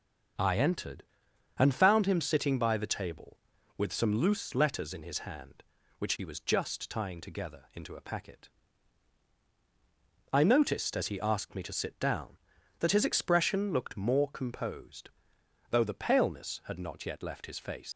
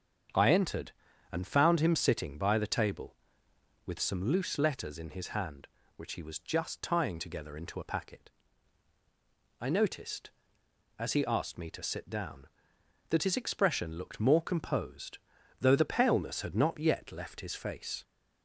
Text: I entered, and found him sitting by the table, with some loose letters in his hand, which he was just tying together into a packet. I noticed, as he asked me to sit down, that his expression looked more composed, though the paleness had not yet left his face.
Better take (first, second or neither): second